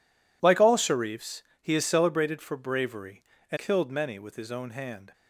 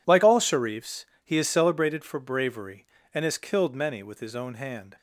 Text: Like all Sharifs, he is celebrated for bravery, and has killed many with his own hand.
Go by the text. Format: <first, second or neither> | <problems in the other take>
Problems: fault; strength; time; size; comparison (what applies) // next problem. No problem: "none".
second | skips "has"; at 3.5 s